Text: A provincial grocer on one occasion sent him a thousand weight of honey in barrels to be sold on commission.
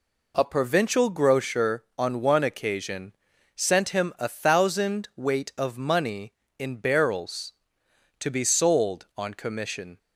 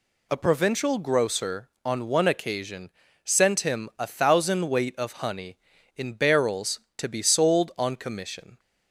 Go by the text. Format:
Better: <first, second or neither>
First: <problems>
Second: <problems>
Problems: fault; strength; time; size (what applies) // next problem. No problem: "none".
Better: second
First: pauses between "occasion" and "sent"; at 3.1 s; 0.42 s long // says "money" for "honey"; at 5.7 s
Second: pauses between "occasion" and "sent"; slight; at 2.9 s; 0.34 s long